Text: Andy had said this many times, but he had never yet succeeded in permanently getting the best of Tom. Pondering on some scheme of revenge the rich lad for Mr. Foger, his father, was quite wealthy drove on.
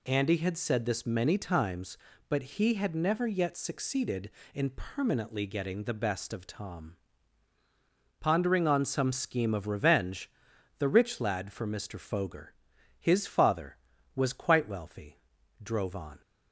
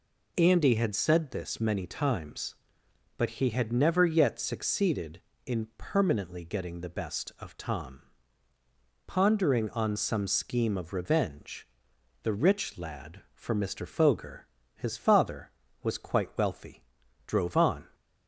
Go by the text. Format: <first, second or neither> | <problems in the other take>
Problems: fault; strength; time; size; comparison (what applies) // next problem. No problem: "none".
neither | pauses between "revenge" and "the"; noticeable; the same in both // pauses between "wealthy" and "drove"; the same in both